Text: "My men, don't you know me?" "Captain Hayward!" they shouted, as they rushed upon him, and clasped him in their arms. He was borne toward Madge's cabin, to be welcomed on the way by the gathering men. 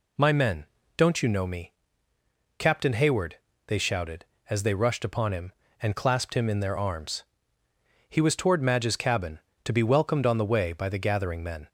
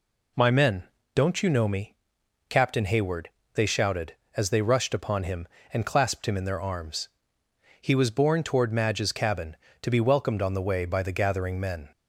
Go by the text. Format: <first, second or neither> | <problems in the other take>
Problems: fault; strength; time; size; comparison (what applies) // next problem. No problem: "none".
second | skips "borne"; at 8.3 s